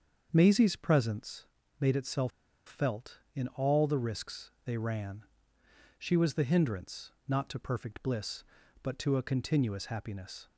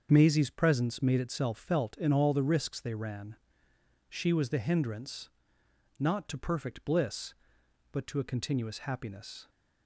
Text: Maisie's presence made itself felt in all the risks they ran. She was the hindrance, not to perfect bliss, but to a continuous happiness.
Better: second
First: starts louder than the rest; until 1.3 s; 7 dB // pauses between "presence" and "made"; slight; at 1.4 s; 0.36 s long // pauses between "itself" and "felt"; slight; at 2.3 s; 0.35 s long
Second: starts louder than the rest; until 1.1 s; 7 dB

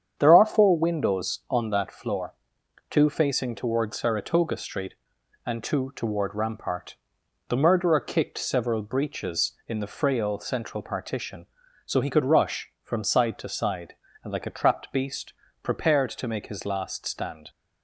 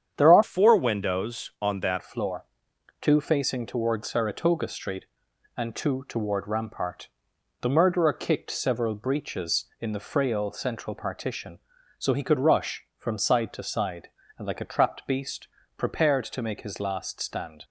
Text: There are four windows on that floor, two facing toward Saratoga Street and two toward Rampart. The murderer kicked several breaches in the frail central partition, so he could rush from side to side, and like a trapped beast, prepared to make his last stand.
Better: first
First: starts louder than the rest; strong; until 1.1 s; 8.5 dB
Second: starts louder than the rest; strong; until 1.1 s; 8.5 dB // changes voice from "four" to "that"; from 0.4 to 2.0 s; 1.6 s long

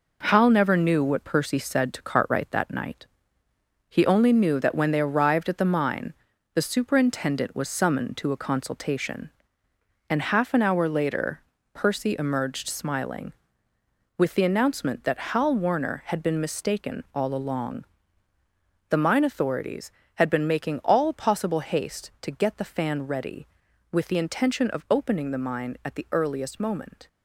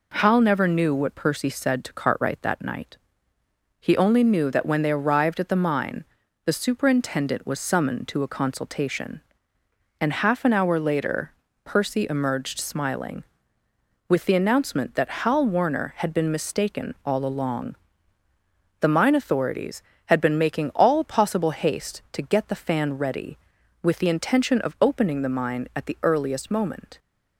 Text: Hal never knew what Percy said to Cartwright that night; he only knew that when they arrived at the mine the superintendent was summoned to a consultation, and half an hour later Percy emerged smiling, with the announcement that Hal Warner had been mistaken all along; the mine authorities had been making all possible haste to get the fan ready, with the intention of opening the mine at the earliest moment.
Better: second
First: gets quieter; noticeable; throughout; 6 dB // pauses between "mine" and "the"; at 6.1 s; 0.40 s long // pauses between "later" and "Percy"; slight; at 11.4 s; 0.32 s long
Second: pauses between "mine" and "the"; at 6.0 s; 0.40 s long // pauses between "later" and "Percy"; slight; at 11.3 s; 0.32 s long

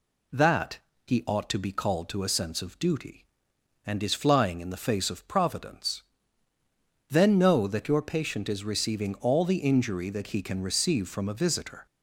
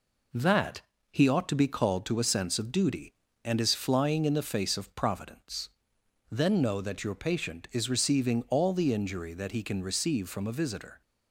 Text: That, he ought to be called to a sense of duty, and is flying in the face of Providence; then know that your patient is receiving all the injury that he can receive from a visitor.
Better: first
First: none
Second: gets quieter; throughout; 4 dB

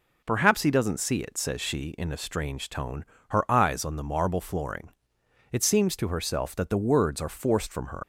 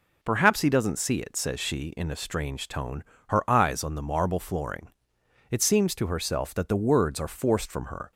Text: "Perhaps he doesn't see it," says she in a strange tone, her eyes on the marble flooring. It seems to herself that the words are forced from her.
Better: second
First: leaves "her" unfinished; at 8.0 s; 90 ms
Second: none

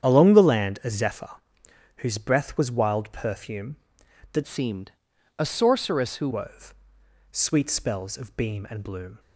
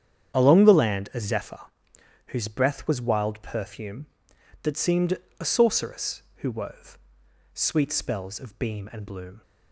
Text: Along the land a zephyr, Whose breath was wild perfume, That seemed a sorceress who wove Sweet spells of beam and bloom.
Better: second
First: starts louder than the rest; strong; until 1.1 s; 8.5 dB // changes voice from "seemed" to "who"; from 4.4 to 6.2 s; 1.8 s long // pauses between "seemed" and "a"; noticeable; at 4.9 s; 0.48 s long // pauses between "wove" and "Sweet"; noticeable; at 6.7 s; 0.58 s long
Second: starts louder than the rest; strong; until 1.4 s; 8.5 dB // pauses between "seemed" and "a"; slight; at 5.1 s; 0.22 s long // pauses between "wove" and "Sweet"; noticeable; at 6.9 s; 0.56 s long

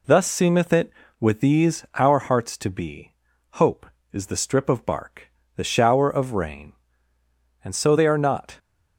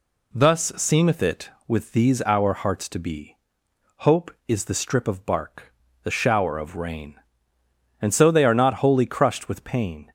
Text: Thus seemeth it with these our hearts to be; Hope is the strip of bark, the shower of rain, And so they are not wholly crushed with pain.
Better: second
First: stops before "wholly crushed with pain"; at 8.5 s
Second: none

